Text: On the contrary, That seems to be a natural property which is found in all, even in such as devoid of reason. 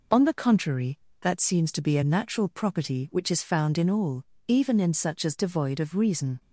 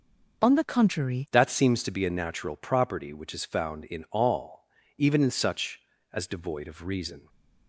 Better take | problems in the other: first | starts louder than the rest; until 1.4 s; 6.5 dB // changes voice at "That"; from 1.3 s on; 5.9 s long

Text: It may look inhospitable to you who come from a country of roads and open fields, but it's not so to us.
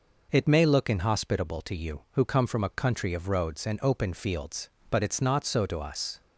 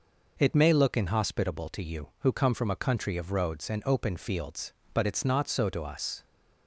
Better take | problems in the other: neither | none

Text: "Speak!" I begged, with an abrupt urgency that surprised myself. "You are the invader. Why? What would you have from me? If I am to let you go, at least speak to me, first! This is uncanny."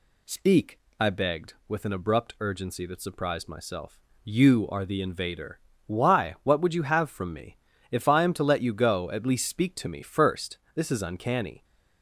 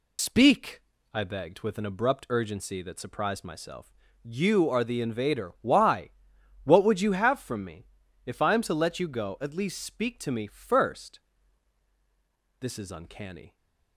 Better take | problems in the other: first | loses the start of "Speak"; at 0.1 s; 105 ms

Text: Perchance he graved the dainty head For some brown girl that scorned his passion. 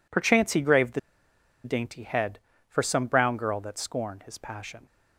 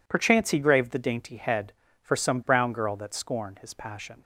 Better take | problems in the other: second | pauses between "the" and "dainty"; noticeable; at 0.9 s; 0.64 s long

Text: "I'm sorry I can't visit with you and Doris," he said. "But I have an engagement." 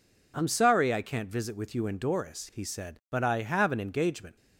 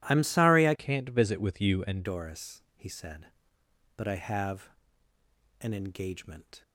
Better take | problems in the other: first | changes voice from "can't" to "and"; from 0.7 to 2.0 s; 1.3 s long // pauses between "have" and "an"; noticeable; at 4.6 s; 0.92 s long

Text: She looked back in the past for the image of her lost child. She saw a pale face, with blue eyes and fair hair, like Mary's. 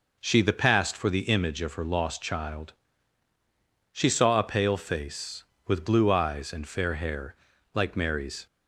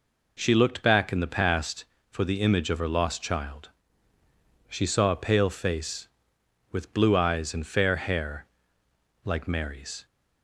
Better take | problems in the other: second | skips "looked back in"; at 0.4 s

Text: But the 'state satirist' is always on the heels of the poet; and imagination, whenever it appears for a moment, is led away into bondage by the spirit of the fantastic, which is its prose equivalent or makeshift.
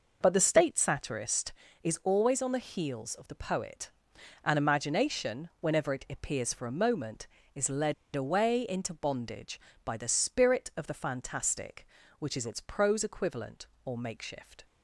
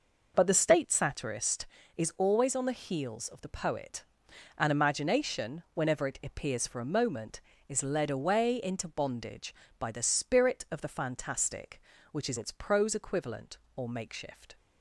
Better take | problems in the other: second | pauses between "led" and "away"; slight; at 7.9 s; 0.20 s long

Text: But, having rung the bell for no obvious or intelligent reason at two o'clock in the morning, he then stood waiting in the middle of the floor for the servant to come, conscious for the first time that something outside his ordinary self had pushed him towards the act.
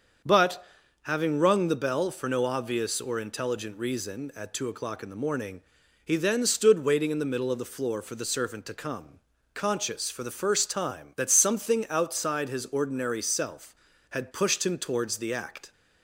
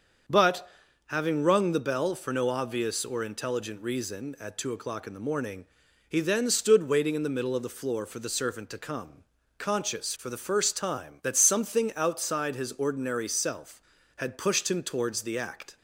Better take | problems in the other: neither | starts louder than the rest; the same in both

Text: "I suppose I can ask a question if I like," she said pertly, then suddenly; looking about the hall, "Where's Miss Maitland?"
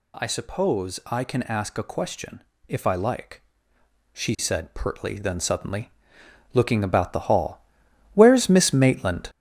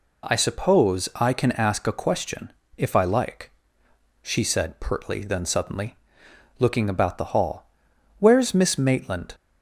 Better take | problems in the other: second | gets louder; noticeable; throughout; 5.5 dB // pauses between "question" and "if"; slight; at 2.4 s; 0.28 s long; slight in the second

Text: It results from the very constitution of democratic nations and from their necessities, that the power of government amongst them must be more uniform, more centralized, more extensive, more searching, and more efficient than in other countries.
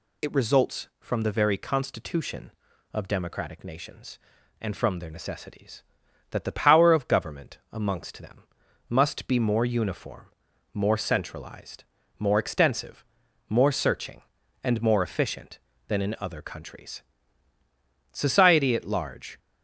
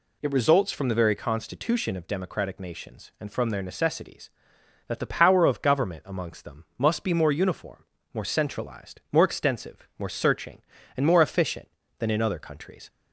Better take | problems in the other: second | pauses between "them" and "must"; at 8.4 s; 0.44 s long // goes on to say "Society at large"; noticeable; from 18.1 s on; 1.2 s long

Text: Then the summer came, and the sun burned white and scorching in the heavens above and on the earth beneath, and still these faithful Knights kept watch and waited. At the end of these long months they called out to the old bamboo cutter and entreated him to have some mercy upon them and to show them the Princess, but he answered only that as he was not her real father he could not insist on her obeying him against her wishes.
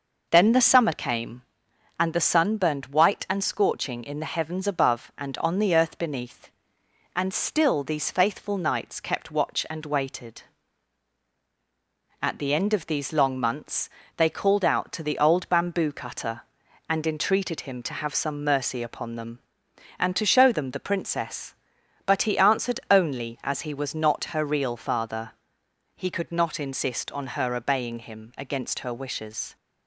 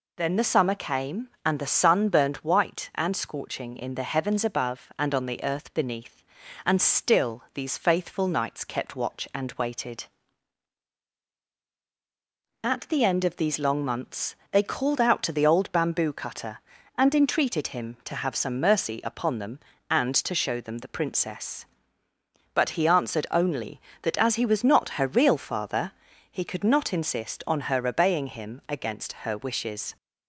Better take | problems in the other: second | pauses between "months" and "they"; slight; at 13.8 s; 0.30 s long; slight in the second // skips "that"; at 23.4 s // pauses between "father" and "he"; noticeable; at 25.3 s; 0.64 s long; also in the second

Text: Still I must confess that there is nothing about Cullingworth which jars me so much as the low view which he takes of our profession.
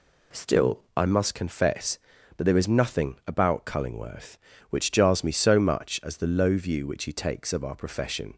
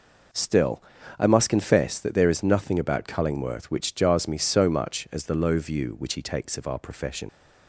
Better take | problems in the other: first | pauses between "Still" and "I"; slight; at 0.8 s; 0.36 s long // leaves "profession" unfinished; at 7.2 s; 50 ms

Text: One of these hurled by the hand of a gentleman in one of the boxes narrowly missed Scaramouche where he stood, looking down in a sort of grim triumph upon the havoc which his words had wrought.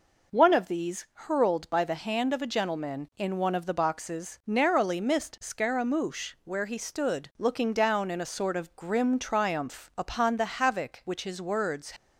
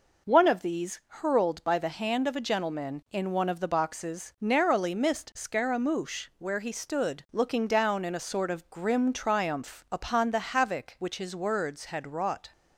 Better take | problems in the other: second | stops before "had wrought"; at 11.9 s

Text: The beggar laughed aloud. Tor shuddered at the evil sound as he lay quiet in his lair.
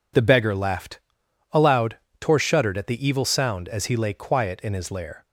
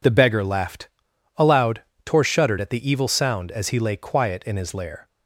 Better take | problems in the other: neither | pauses between "laughed" and "aloud"; noticeable; the same in both

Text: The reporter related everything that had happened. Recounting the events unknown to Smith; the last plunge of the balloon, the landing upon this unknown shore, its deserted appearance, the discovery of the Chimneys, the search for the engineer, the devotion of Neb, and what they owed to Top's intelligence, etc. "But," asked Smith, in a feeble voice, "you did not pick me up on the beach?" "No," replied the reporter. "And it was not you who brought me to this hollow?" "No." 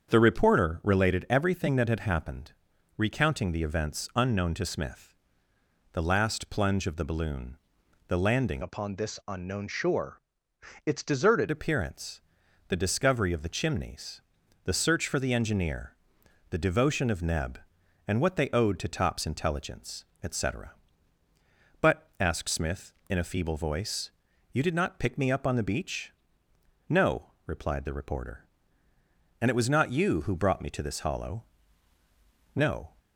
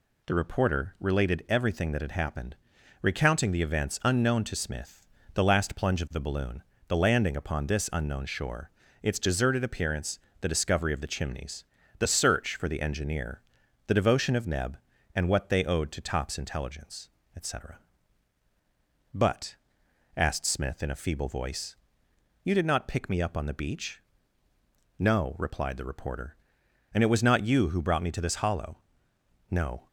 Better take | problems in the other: second | starts louder than the rest; strong; until 1.1 s; 7 dB // changes voice from "upon" to "deserted"; from 8.6 to 11.4 s; 2.8 s long

